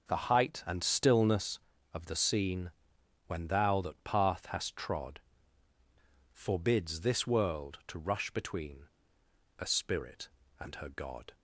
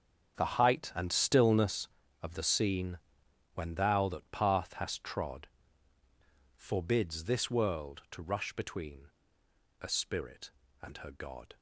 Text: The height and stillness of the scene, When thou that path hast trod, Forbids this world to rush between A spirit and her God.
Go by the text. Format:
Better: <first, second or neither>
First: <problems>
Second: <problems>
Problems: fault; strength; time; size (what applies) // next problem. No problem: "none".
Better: first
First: pauses between "between" and "A"; noticeable; at 8.8 s; 0.72 s long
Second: gets quieter; strong; throughout; 15 dB // pauses between "between" and "A"; noticeable; at 9.1 s; 0.72 s long